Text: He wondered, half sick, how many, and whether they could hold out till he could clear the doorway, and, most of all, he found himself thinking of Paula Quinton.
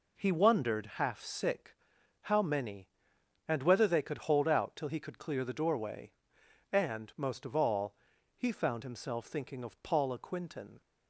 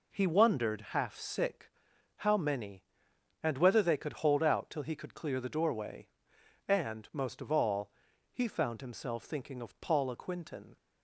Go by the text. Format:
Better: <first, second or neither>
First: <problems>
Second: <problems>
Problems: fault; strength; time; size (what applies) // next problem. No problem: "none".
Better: neither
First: none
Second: none